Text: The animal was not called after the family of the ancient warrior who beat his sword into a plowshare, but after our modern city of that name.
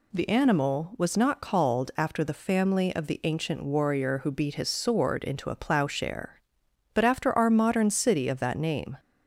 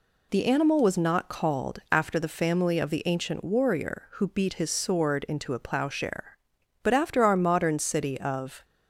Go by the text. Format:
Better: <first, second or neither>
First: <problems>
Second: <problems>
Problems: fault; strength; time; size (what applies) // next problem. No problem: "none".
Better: first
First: none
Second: stops before "that name"; at 8.6 s